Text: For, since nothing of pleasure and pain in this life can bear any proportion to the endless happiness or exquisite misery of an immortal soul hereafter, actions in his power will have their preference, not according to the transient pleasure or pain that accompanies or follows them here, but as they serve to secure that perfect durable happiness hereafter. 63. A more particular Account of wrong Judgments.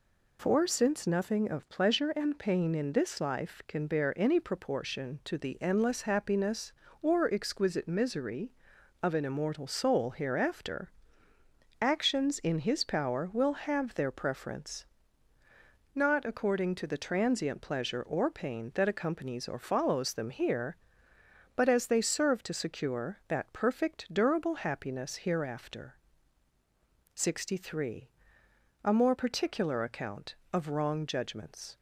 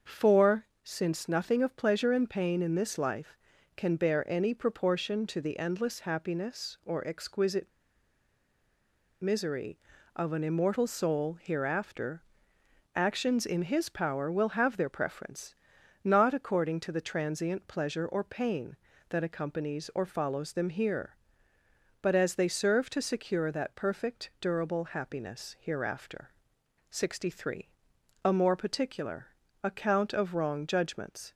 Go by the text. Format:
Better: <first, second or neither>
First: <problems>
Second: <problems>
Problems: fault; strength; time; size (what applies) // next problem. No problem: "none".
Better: first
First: none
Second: starts louder than the rest; until 1.2 s; 7 dB // pauses between "exquisite" and "misery"; strong; at 7.6 s; 1.5 s long // pauses between "particular" and "Account"; slight; at 29.2 s; 0.36 s long